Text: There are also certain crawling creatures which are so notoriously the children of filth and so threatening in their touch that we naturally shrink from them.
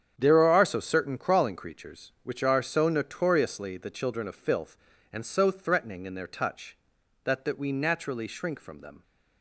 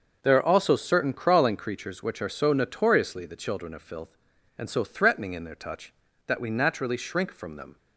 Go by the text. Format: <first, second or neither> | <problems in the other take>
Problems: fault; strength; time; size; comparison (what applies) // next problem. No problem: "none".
second | starts louder than the rest; strong; until 1.1 s; 8 dB; also in the second // says "that" twice; at 7.4 s